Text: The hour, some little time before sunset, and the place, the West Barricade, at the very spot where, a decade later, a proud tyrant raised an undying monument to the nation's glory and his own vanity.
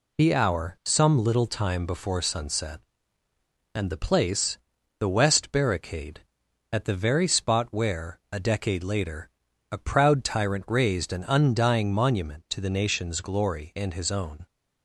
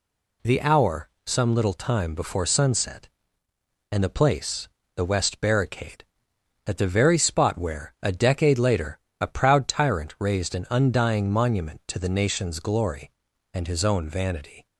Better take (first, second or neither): second